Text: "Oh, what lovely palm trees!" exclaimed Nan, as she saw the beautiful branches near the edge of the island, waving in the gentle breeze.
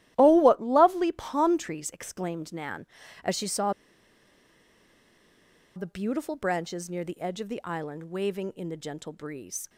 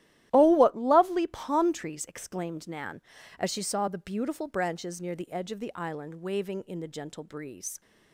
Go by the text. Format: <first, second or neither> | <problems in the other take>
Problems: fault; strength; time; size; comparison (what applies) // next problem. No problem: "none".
second | starts louder than the rest; strong; until 1.1 s; 14 dB; strong in the second // pauses between "saw" and "the"; strong; at 3.7 s; 2.0 s long